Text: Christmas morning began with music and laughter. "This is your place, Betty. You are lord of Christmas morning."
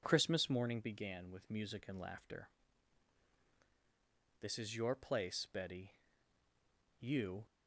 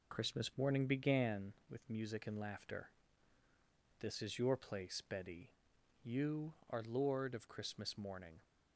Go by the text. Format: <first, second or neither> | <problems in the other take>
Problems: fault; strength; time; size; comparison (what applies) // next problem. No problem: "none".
second | stops before "are lord of Christmas morning"; at 7.4 s